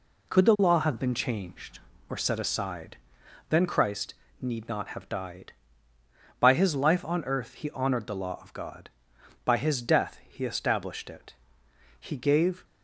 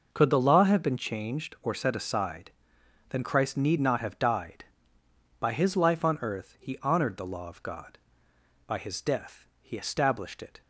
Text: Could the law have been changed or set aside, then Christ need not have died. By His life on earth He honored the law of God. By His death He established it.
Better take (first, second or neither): second